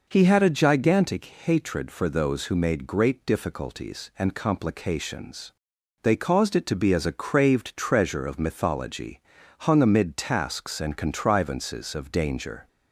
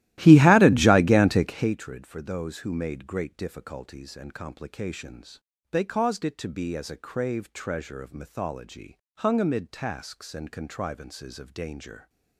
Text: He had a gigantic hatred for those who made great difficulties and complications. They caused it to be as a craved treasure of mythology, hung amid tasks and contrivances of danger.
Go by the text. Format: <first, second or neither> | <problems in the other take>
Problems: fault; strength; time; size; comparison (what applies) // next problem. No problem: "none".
first | starts louder than the rest; strong; until 1.7 s; 15.5 dB